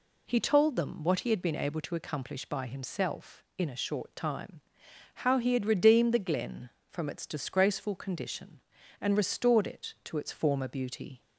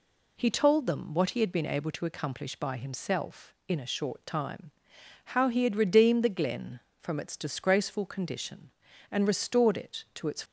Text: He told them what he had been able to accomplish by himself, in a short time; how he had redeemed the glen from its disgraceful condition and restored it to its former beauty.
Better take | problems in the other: first | stops before "former beauty"; at 10.4 s

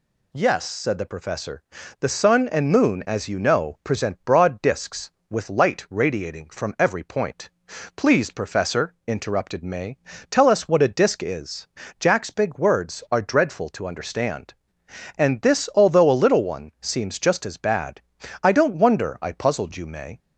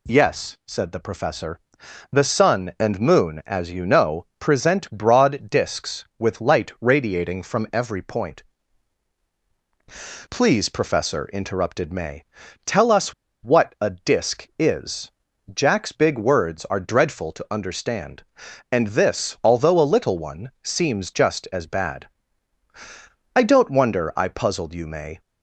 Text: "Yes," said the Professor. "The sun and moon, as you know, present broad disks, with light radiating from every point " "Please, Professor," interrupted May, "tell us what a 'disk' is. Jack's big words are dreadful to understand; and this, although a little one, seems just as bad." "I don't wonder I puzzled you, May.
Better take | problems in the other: first | pauses between "us" and "what"; slight; at 13.1 s; 0.31 s long

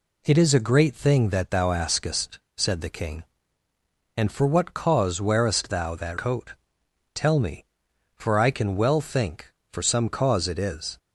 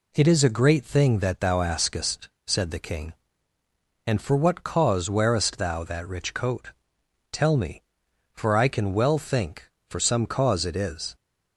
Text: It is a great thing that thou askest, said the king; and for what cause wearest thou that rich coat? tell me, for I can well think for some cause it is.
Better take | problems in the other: second | skips "rich"; at 6.1 s

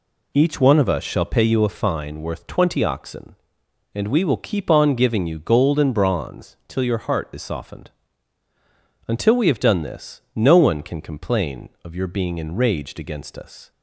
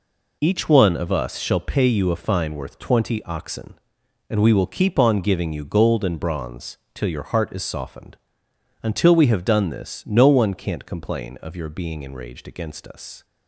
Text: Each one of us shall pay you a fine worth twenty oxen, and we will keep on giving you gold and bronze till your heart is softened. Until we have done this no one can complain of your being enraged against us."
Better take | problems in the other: first | pauses between "bronze" and "till"; slight; at 6.7 s; 0.16 s long // says "can't" for "can"; at 10.5 s

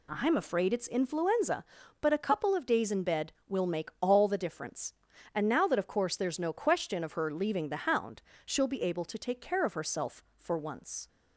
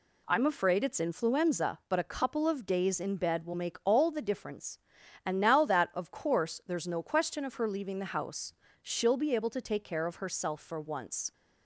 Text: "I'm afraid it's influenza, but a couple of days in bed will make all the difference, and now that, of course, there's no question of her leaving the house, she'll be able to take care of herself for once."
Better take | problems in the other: second | says "hound" for "house"; at 7.8 s

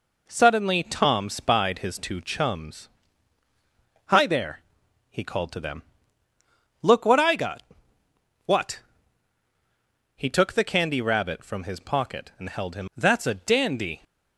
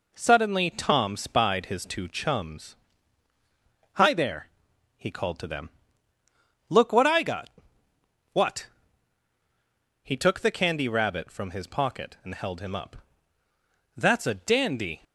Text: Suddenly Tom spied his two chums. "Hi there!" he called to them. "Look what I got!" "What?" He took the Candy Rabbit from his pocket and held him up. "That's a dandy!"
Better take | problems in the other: second | skips "up"; at 12.9 s

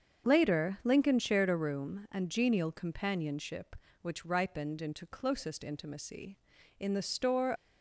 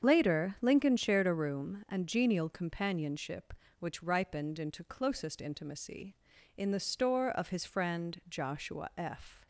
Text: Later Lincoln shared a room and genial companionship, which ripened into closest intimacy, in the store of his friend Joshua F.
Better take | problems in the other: second | starts louder than the rest; until 1.3 s; 7 dB; strong in the second // stops before "of his friend Joshua F"; at 7.5 s

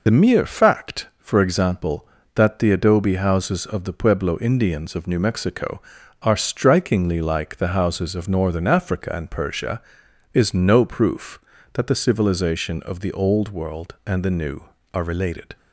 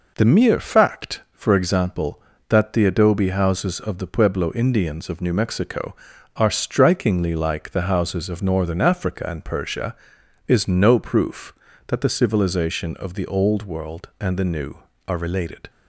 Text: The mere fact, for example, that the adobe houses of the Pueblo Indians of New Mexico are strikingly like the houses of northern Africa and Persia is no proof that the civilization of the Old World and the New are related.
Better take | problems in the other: second | loses the start of "The"; at 0.0 s; 40 ms

